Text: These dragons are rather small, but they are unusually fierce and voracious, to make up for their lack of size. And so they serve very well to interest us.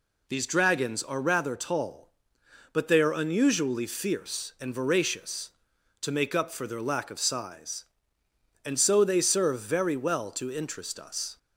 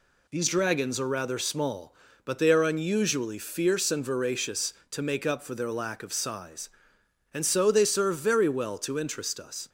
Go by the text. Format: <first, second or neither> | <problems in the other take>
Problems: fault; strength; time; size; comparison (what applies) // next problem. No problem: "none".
second | says "tall" for "small"; at 1.5 s